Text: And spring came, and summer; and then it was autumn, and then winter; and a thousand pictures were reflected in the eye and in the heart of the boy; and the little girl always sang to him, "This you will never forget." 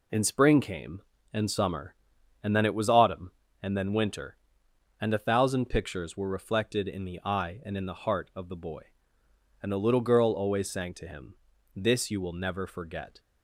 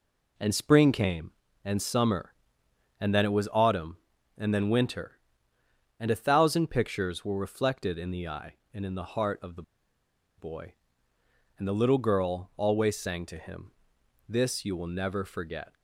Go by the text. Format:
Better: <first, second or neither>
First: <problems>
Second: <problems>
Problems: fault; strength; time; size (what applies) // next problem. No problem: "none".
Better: first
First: none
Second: pauses between "the" and "boy"; noticeable; at 9.6 s; 0.75 s long